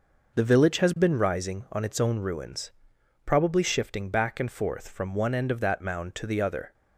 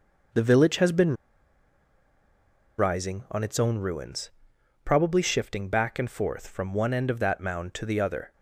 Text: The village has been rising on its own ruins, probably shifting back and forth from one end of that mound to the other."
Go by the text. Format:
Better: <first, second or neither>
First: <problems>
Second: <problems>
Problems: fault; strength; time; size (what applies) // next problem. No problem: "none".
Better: first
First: none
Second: pauses between "been" and "rising"; strong; at 1.1 s; 1.6 s long